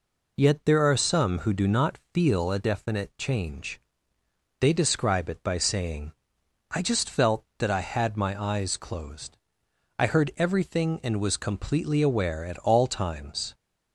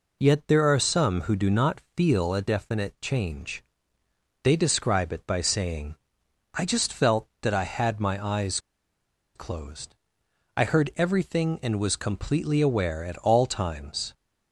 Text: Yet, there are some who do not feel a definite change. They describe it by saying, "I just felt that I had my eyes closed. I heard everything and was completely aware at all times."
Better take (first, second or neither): first